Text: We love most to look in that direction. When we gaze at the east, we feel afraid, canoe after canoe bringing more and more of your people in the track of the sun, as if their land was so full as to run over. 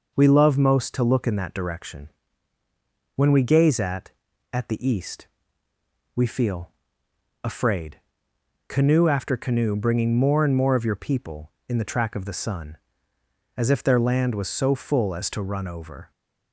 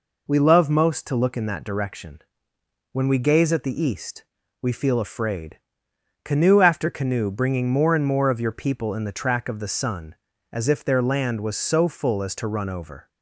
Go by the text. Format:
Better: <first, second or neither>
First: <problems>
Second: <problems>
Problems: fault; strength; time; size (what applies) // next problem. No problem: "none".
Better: second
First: says "at" twice; at 4.5 s // pauses between "feel" and "afraid"; noticeable; at 6.6 s; 0.74 s long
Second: none